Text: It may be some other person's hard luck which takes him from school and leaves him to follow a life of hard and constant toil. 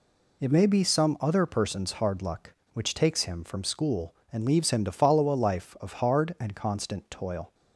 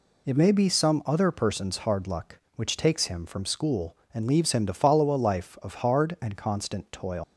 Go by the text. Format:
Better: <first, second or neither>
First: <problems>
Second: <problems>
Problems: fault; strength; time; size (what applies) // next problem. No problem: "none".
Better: first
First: none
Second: leaves "toil" unfinished; at 7.2 s; 120 ms